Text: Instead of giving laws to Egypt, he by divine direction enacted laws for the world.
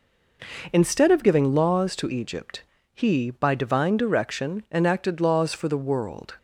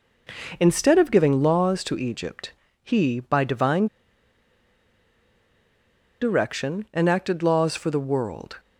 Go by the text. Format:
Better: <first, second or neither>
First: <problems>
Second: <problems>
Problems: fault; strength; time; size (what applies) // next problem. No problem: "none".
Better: first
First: none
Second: pauses between "divine" and "direction"; strong; at 3.8 s; 2.3 s long